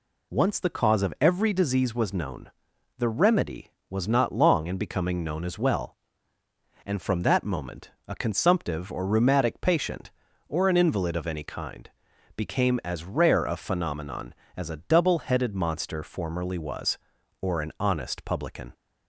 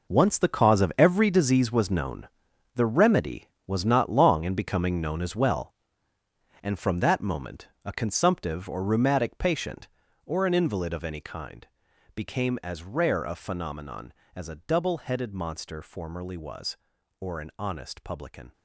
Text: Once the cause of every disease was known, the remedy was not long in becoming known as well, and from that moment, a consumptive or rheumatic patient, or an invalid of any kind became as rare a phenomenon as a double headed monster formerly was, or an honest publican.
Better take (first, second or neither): first